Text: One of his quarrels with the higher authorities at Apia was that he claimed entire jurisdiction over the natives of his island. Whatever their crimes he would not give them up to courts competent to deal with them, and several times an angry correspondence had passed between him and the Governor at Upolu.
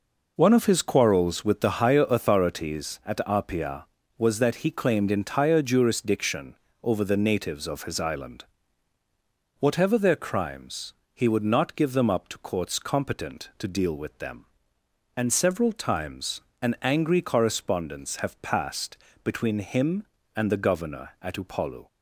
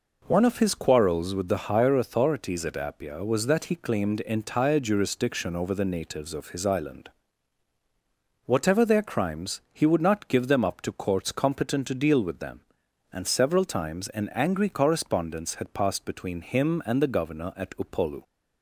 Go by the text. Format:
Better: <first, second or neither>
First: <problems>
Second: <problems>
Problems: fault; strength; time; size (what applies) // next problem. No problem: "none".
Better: second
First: pauses between "jurisdiction" and "over"; slight; at 6.5 s; 0.28 s long // pauses between "crimes" and "he"; slight; at 10.9 s; 0.22 s long // pauses between "times" and "an"; slight; at 16.4 s; 0.20 s long // says "have" for "had"; at 18.1 s // pauses between "passed" and "between"; slight; at 18.9 s; 0.28 s long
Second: none